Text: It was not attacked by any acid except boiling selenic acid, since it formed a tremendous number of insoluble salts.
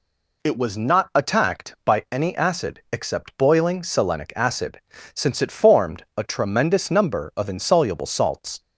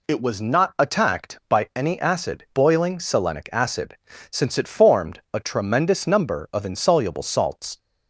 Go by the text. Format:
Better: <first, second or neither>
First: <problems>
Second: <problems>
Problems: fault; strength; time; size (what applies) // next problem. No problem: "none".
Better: first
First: none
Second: skips "except"; at 2.4 s